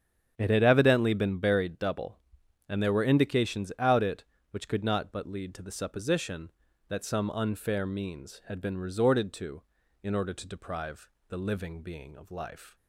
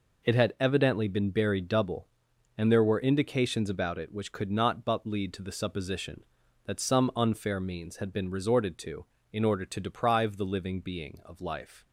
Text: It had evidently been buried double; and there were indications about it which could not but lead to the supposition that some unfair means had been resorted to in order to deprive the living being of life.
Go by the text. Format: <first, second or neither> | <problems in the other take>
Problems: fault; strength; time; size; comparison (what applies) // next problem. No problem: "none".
second | starts louder than the rest; strong; until 1.3 s; 8.5 dB // says "out" for "about"; at 3.7 s // pauses between "deprive" and "the"; slight; at 11.0 s; 0.20 s long